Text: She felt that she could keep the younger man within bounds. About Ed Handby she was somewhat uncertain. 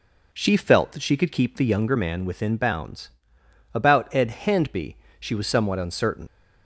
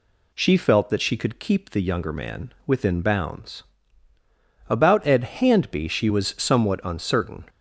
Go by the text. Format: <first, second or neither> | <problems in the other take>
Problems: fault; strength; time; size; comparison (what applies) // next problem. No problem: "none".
second | pauses between "Ed" and "Handby"; slight; at 4.2 s; 0.16 s long; slight in the second // pauses between "Handby" and "she"; slight; at 4.9 s; 0.24 s long // leaves "uncertain" unfinished; at 6.2 s; 55 ms